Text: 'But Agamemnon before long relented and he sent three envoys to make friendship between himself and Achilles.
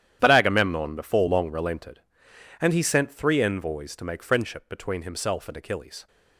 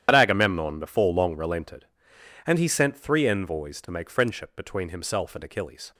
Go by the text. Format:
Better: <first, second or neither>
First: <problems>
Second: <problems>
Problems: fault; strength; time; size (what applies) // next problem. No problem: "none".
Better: first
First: starts louder than the rest; strong; until 1.2 s; 11 dB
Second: loses the start of "But"; at 0.0 s; 45 ms // starts louder than the rest; strong; until 1.0 s; 10.5 dB